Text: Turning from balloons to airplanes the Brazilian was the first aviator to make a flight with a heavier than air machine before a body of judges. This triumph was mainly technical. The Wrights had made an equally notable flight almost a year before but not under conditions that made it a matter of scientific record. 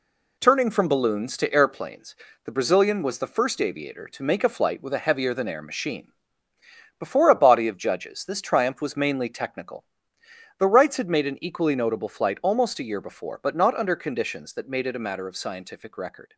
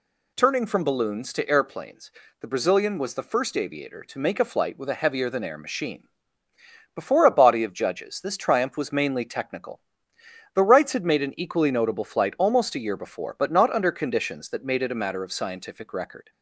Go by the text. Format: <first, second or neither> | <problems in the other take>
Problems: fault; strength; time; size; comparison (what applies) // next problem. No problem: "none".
second | gets quieter; throughout; 6 dB // pauses between "airplanes" and "the"; slight; at 2.1 s; 0.30 s long; slight in the second // pauses between "machine" and "before"; noticeable; at 6.1 s; 0.88 s long; noticeable in the second